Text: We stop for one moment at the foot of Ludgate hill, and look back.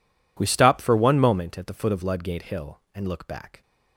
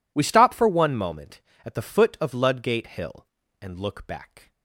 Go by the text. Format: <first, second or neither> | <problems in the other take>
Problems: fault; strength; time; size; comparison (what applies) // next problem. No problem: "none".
neither | none